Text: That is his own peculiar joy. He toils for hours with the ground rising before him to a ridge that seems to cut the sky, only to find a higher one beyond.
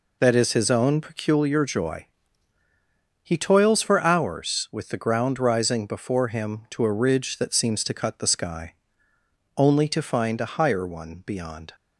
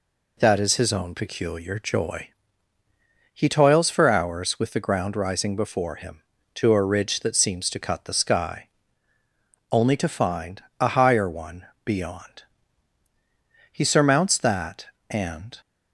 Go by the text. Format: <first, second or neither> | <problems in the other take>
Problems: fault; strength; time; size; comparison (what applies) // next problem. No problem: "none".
first | pauses between "find" and "a"; slight; at 10.6 s; 0.18 s long // pauses between "one" and "beyond"; slight; at 11.6 s; 0.18 s long // goes on to say "He surmounts that and"; strong; from 13.7 s on; 1.8 s long